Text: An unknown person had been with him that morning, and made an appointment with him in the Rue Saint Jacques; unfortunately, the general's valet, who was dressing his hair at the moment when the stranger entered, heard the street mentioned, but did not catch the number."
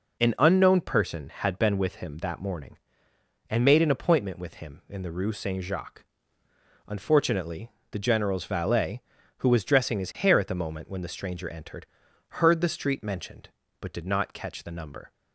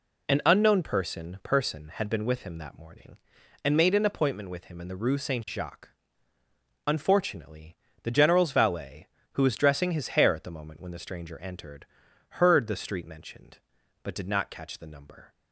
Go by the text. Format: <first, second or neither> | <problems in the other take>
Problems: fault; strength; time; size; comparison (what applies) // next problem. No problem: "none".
first | says "person" twice; at 1.4 s